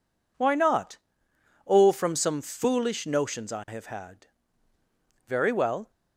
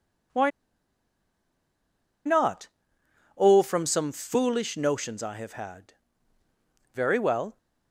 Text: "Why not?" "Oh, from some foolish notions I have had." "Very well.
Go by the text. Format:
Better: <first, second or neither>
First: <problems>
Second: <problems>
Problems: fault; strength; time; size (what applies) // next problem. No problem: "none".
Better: first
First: none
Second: pauses between "Why" and "not"; strong; at 0.5 s; 1.7 s long